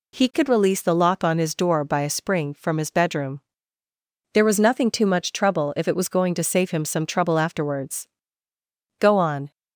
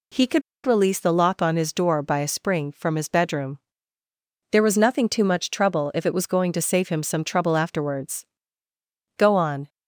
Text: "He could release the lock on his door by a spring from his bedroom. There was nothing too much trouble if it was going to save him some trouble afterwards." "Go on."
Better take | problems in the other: first | pauses between "could" and "release"; slight; at 0.4 s; 0.25 s long

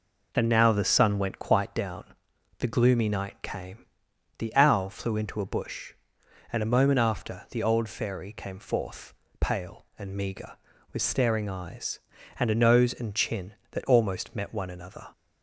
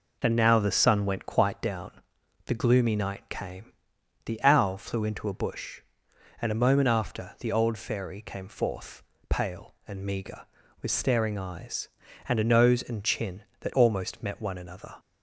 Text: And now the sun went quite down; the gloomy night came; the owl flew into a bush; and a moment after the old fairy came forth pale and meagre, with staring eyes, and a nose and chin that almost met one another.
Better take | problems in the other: neither | pauses between "forth" and "pale"; slight; the same in both

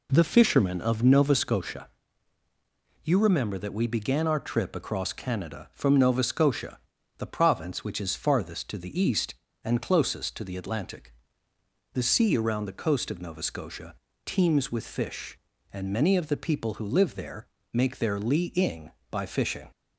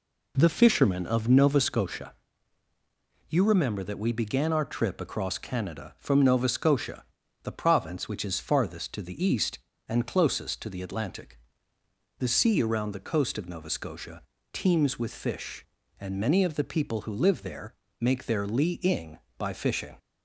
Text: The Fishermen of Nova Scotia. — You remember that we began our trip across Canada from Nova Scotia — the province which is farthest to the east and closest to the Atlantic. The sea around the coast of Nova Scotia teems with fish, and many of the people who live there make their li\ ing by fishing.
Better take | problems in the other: neither | pauses between "Scotia" and "teems"; slight; the same in both // pauses between "there" and "make"; slight; the same in both

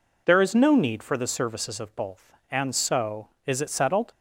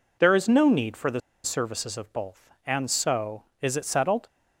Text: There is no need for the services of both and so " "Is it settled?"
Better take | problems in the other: first | pauses between "the" and "services"; slight; at 1.2 s; 0.23 s long

